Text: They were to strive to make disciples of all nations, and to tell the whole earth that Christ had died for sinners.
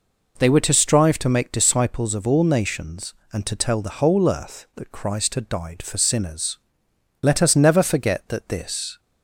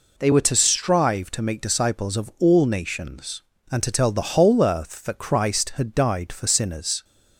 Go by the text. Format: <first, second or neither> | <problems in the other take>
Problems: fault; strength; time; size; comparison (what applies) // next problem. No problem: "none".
second | goes on to say "Let us never forget that this"; strong; from 7.2 s on; 1.7 s long